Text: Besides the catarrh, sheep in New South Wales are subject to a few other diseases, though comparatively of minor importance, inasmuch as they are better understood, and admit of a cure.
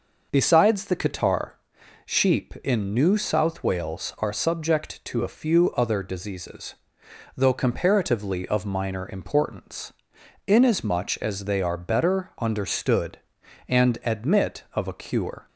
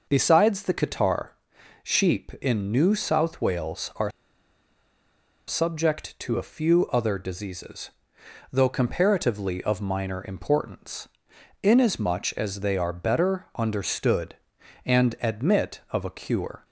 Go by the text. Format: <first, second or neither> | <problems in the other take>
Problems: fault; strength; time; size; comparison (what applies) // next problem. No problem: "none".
first | pauses between "are" and "subject"; strong; at 4.0 s; 1.3 s long